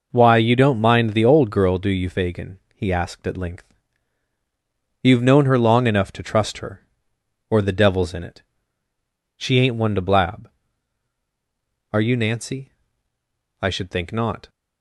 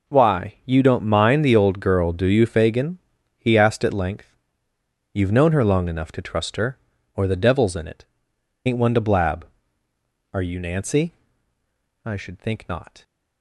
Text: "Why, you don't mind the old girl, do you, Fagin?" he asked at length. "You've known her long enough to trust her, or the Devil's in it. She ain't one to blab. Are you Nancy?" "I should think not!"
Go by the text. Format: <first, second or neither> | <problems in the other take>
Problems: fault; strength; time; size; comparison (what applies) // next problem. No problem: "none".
first | skips "She"; at 8.3 s